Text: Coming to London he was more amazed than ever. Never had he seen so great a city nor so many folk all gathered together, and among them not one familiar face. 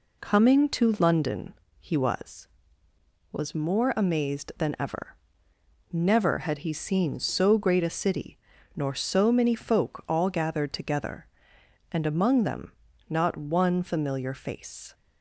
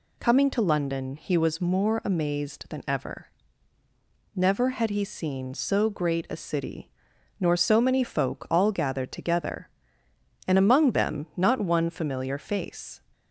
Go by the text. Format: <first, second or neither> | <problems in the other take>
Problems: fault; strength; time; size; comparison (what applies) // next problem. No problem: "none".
second | pauses between "London" and "he"; slight; at 1.5 s; 0.26 s long // says "was" twice; at 3.3 s // pauses between "city" and "nor"; at 8.3 s; 0.38 s long; noticeable in the second // pauses between "them" and "not"; slight; at 12.7 s; 0.36 s long